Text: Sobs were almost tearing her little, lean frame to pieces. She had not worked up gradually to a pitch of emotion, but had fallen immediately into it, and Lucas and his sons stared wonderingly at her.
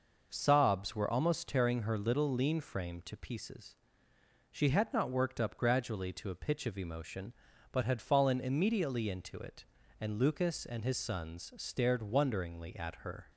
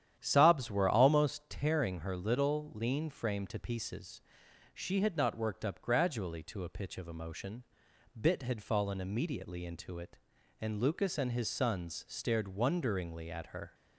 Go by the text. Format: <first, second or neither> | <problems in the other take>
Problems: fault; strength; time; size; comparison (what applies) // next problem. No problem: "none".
first | starts louder than the rest; strong; until 1.2 s; 10 dB // says "bit" for "but"; at 8.1 s